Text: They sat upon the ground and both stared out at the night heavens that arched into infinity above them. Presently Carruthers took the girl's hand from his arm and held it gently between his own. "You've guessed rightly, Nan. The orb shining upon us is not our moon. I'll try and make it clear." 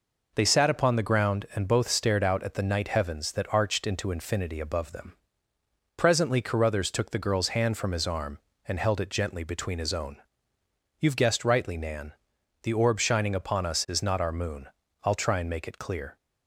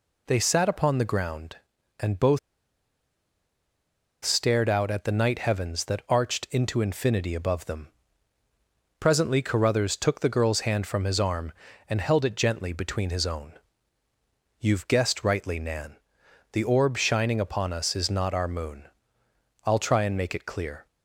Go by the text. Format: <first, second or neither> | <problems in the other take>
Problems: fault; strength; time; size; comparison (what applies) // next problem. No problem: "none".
first | pauses between "both" and "stared"; strong; at 2.3 s; 1.8 s long